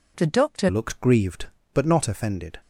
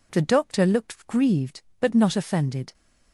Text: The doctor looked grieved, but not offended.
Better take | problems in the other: second | changes voice at "looked"; from 0.6 s on; 1.9 s long

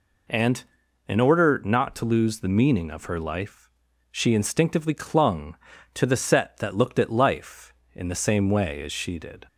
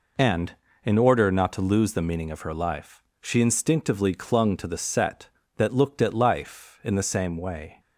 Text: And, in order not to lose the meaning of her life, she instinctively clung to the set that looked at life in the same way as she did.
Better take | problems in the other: first | stops before "as she did"; at 7.7 s

